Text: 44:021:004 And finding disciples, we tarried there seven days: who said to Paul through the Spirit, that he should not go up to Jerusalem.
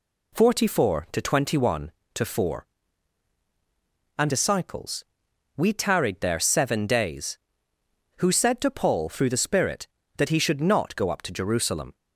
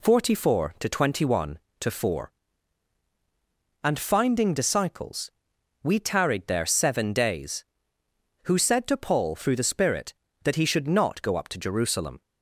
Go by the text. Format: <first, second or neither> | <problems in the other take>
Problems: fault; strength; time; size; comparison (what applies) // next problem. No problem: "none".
second | skips "finding"; at 4.3 s